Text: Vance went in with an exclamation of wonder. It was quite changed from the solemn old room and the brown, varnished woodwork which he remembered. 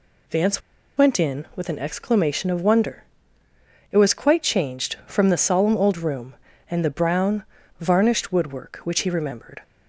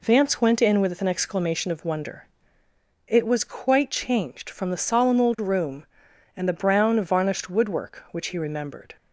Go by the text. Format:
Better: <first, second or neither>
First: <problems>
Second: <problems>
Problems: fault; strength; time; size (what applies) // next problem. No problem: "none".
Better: second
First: pauses between "Vance" and "went"; at 0.6 s; 0.36 s long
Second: none